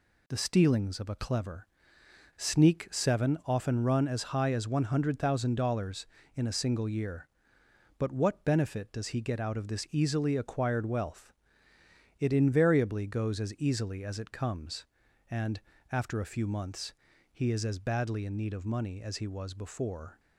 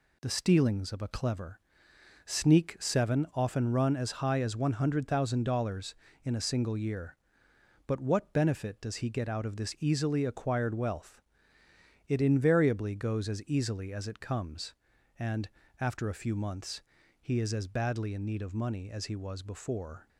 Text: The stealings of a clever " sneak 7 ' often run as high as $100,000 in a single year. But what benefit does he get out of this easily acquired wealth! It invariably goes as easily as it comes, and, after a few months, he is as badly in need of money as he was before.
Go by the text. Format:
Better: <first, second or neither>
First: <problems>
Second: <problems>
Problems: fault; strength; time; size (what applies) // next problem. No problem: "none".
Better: neither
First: none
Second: none